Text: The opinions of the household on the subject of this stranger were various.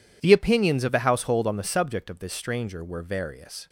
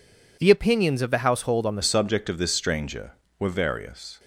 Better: first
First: none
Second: changes voice at "subject"; from 1.8 s on; 2.3 s long

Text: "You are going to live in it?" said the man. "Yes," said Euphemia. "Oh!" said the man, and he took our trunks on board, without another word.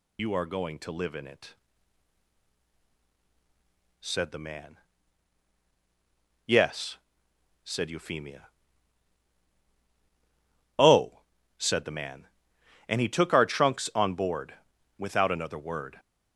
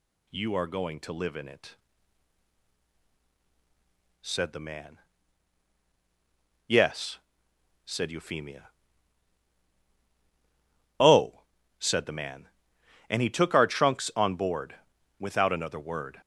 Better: second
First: loses the start of "You"; at 0.1 s; 110 ms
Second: none

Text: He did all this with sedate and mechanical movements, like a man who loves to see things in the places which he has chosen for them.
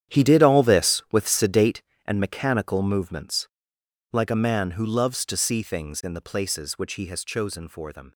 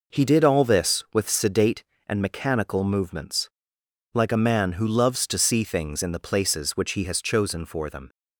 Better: second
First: gets quieter; strong; throughout; 13.5 dB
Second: none

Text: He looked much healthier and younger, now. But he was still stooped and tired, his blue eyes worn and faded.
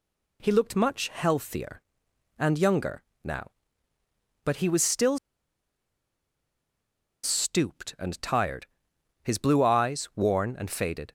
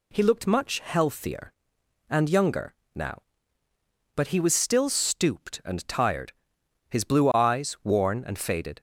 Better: second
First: pauses between "still" and "stooped"; strong; at 5.1 s; 2.0 s long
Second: none

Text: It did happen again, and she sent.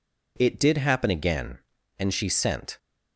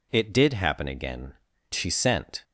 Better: first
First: none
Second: skips "and"; at 1.5 s

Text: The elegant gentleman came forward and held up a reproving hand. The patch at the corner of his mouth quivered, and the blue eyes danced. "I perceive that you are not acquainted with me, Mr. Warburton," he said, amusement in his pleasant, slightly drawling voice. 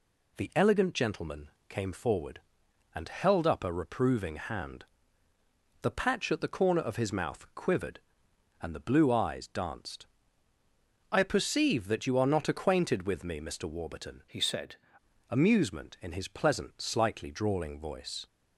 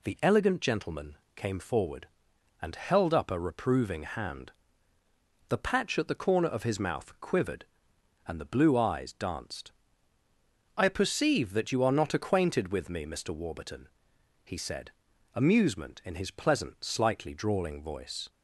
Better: second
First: pauses between "gentleman" and "came"; slight; at 1.4 s; 0.18 s long // changes voice from "he" to "said"; from 14.2 to 14.7 s; 0.5 s long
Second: pauses between "gentleman" and "came"; slight; at 1.1 s; 0.18 s long

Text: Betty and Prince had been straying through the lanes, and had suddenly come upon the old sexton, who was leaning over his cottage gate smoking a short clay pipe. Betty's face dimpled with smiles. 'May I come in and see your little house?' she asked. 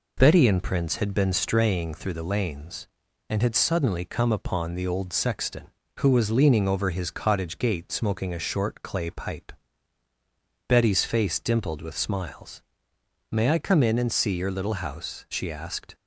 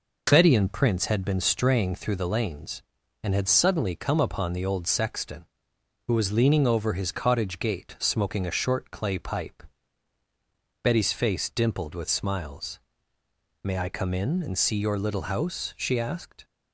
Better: neither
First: none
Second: none

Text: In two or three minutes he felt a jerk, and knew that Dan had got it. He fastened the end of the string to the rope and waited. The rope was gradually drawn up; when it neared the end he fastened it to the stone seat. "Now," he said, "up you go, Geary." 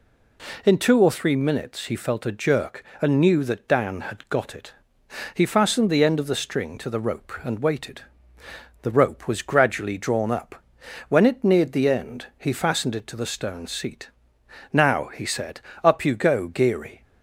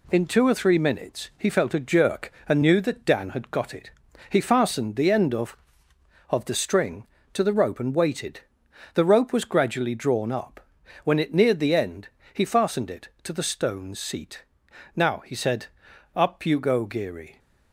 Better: first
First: none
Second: says "of" twice; at 6.2 s // pauses between "end" and "he"; slight; at 12.0 s; 0.24 s long

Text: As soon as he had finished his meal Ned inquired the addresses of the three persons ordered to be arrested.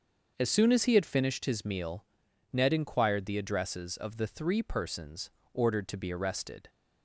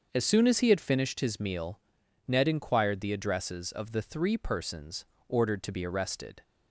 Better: neither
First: starts louder than the rest; until 1.3 s; 6.5 dB // pauses between "meal" and "Ned"; noticeable; at 2.0 s; 0.46 s long // pauses between "persons" and "ordered"; slight; at 5.2 s; 0.24 s long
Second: starts louder than the rest; until 1.1 s; 6.5 dB // pauses between "meal" and "Ned"; noticeable; at 1.8 s; 0.46 s long // pauses between "persons" and "ordered"; slight; at 5.0 s; 0.24 s long

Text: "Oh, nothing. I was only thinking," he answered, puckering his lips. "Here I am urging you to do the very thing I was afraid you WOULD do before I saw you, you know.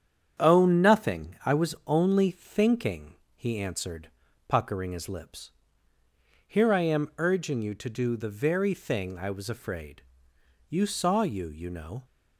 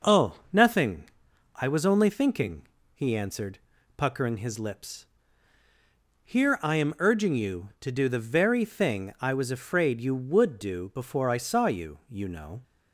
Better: second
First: starts louder than the rest; strong; until 1.4 s; 8.5 dB // pauses between "afraid" and "you"; noticeable; at 10.0 s; 0.66 s long // skips "WOULD do before I"; at 10.8 s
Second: none

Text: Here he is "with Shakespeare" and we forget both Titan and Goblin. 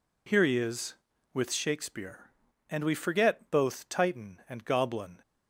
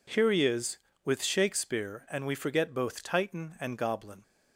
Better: neither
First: none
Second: none

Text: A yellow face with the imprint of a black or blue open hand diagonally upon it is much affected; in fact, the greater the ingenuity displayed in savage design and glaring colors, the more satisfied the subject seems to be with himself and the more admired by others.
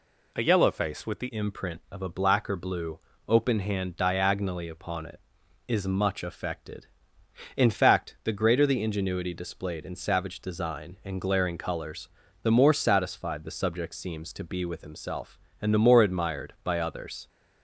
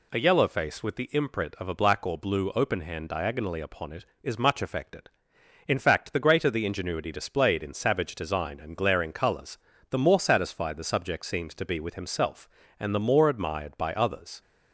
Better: second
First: changes voice at "imprint"; from 1.3 s on; 15.9 s long // pauses between "blue" and "open"; slight; at 2.9 s; 0.30 s long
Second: none

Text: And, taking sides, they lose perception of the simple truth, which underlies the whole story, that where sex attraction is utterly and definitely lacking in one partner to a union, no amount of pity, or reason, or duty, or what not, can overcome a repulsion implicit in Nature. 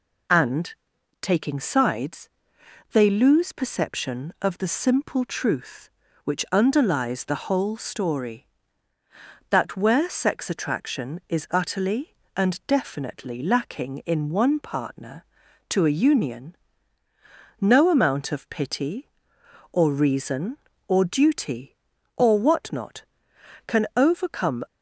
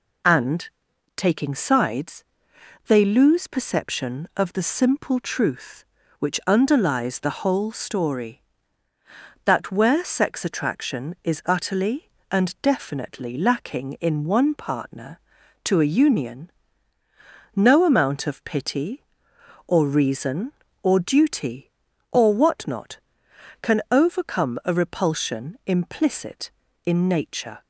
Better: second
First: stops before "a repulsion implicit in Nature"; at 24.6 s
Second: none

